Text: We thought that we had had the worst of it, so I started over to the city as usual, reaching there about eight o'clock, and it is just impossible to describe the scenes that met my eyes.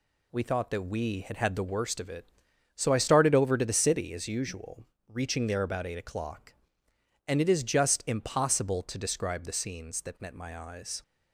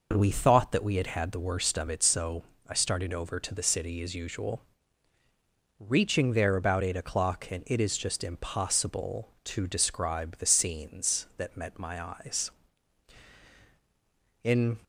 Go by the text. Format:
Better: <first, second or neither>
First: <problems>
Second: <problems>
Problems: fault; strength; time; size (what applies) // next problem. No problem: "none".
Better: first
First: none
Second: pauses between "so" and "I"; slight; at 2.4 s; 0.26 s long // goes on to say "In"; slight; from 14.4 s on; 0.34 s long